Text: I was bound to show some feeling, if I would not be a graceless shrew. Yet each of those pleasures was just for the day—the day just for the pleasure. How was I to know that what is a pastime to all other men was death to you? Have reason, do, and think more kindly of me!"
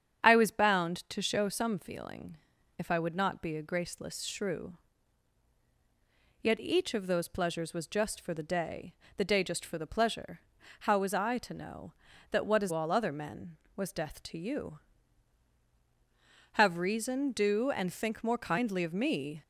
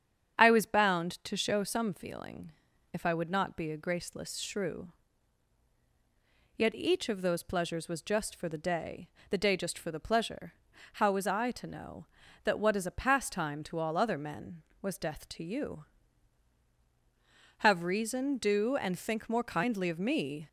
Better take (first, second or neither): second